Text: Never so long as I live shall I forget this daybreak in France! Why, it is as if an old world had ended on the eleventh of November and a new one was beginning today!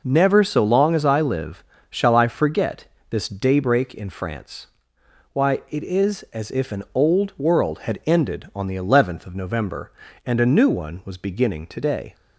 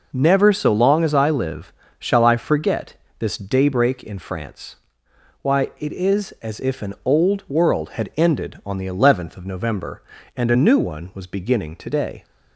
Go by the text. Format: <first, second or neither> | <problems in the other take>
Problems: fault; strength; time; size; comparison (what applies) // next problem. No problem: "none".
neither | pauses between "live" and "shall"; slight; the same in both // pauses between "forget" and "this"; slight; the same in both